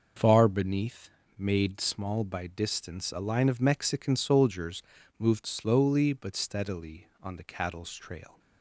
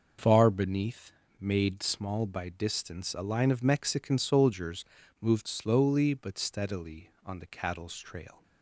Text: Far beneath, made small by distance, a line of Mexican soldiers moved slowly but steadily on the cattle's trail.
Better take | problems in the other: neither | pauses between "soldiers" and "moved"; the same in both

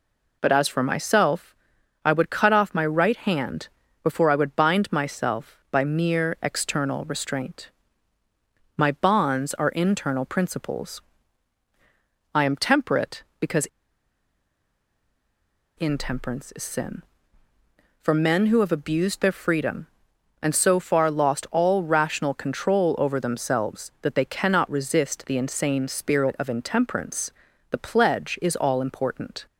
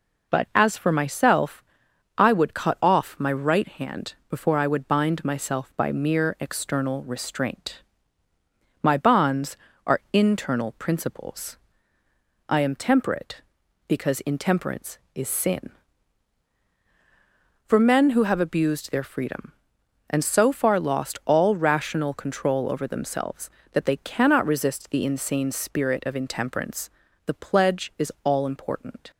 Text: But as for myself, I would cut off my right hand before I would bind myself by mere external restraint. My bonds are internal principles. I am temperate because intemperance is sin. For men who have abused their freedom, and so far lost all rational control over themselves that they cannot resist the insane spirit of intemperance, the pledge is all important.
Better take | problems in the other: second | pauses between "hand" and "before"; slight; at 3.6 s; 0.34 s long // pauses between "because" and "intemperance"; strong; at 13.6 s; 2.1 s long

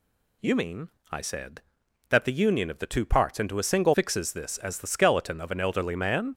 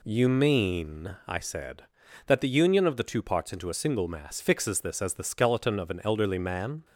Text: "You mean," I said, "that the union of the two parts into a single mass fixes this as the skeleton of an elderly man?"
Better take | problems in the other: second | skips "mass"; at 3.9 s

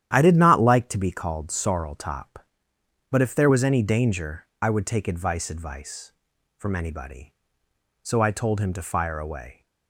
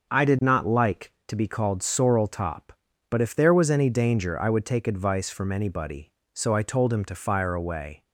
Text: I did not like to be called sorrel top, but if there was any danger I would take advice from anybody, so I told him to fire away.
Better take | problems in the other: second | starts louder than the rest; strong; until 1.1 s; 10.5 dB; noticeable in the second // pauses between "danger" and "I"; slight; at 4.4 s; 0.16 s long // says "advice" twice; at 5.5 s

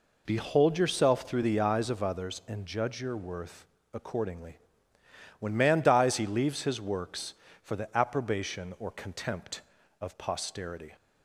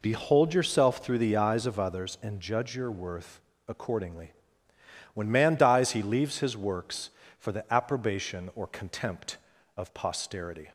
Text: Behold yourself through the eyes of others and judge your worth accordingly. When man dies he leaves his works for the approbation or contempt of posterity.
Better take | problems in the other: neither | pauses between "worth" and "accordingly"; slight; the same in both

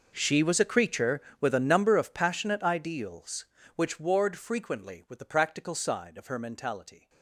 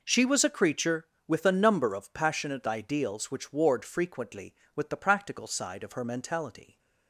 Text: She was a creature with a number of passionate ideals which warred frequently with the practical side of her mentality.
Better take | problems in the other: second | gets quieter; strong; throughout; 19.5 dB

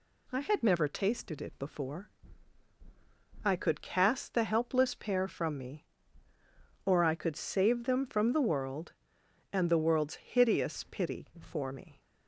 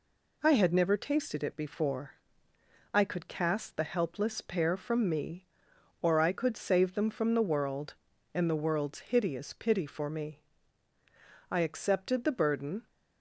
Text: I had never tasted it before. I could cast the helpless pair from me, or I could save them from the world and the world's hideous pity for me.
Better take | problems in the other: first | goes on to say "I accepted the burden"; from 11.4 s on; 1.3 s long

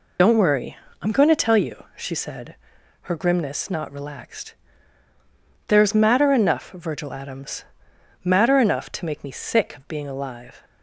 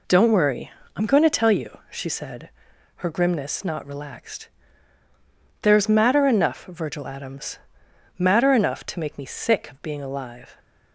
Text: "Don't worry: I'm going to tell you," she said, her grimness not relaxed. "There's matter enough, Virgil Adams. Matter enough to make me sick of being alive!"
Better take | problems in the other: second | loses the start of "Don't"; at 0.1 s; 75 ms

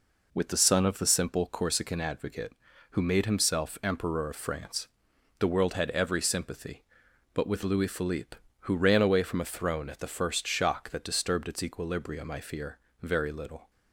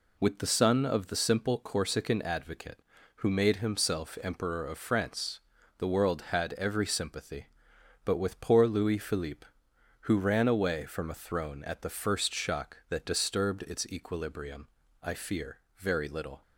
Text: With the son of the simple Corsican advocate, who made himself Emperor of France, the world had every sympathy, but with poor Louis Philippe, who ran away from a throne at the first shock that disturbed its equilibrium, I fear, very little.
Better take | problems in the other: second | skips "poor"; at 7.6 s

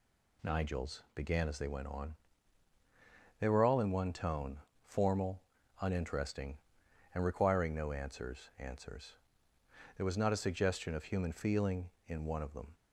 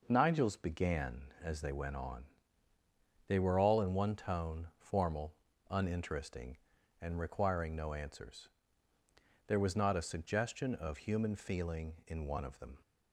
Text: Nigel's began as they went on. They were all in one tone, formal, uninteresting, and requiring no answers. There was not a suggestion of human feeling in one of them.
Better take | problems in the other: second | says "answers" twice; at 8.5 s

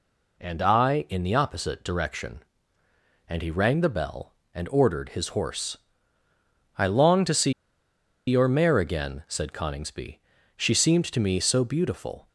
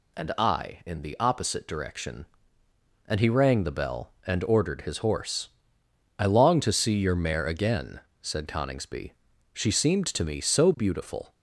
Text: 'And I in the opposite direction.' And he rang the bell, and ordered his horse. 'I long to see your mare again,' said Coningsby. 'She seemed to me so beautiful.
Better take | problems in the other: second | pauses between "see" and "your"; noticeable; at 7.5 s; 0.74 s long

